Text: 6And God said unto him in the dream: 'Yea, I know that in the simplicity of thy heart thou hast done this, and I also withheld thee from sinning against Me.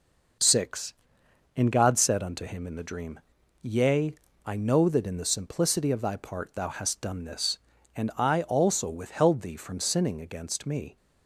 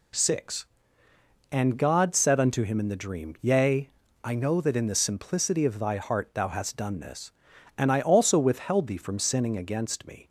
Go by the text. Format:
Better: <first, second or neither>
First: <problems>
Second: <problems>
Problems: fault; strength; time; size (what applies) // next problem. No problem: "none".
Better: second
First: says "part" for "heart"; at 6.1 s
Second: none